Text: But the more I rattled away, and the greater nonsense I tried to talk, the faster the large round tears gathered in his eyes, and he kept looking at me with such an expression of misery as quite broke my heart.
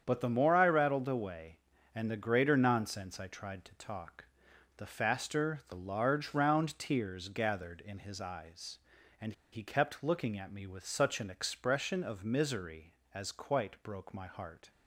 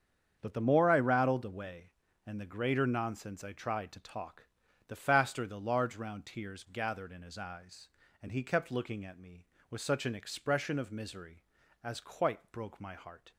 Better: second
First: starts louder than the rest; strong; until 1.0 s; 8 dB // pauses between "and" and "he"; slight; at 9.3 s; 0.20 s long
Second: starts louder than the rest; strong; until 1.4 s; 7.5 dB

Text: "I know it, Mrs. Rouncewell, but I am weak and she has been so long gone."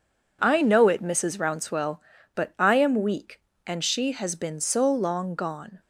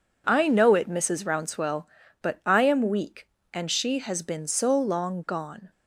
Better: neither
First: none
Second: none

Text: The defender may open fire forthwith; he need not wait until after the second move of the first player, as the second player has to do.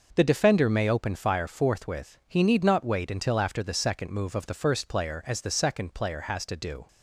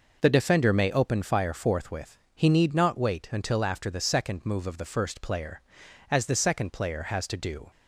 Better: neither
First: none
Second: none

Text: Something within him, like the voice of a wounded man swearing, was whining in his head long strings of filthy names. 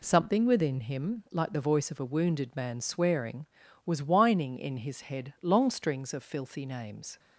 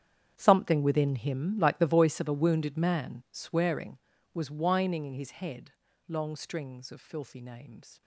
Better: first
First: none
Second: gets quieter; strong; throughout; 16 dB // pauses between "head" and "long"; slight; at 5.7 s; 0.36 s long

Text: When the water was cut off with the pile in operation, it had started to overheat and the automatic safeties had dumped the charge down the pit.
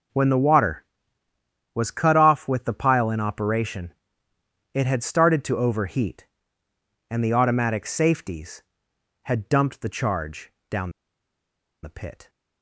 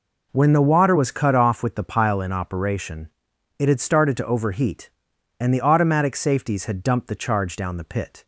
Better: second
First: pauses between "charge" and "down"; slight; at 10.5 s; 0.16 s long // pauses between "down" and "the"; noticeable; at 10.8 s; 0.93 s long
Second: none

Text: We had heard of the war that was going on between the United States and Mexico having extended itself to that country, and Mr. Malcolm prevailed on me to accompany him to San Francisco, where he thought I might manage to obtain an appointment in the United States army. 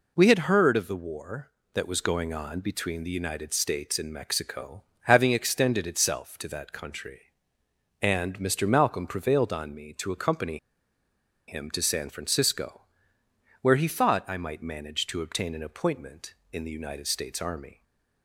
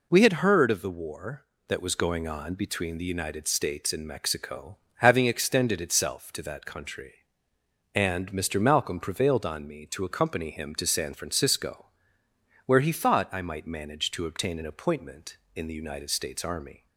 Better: second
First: pauses between "Mexico" and "having"; slight; at 4.8 s; 0.20 s long // pauses between "accompany" and "him"; noticeable; at 10.5 s; 0.91 s long // stays silent after the last word; slight; from 17.7 s on; 0.5 s long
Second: pauses between "Mexico" and "having"; slight; at 4.7 s; 0.20 s long

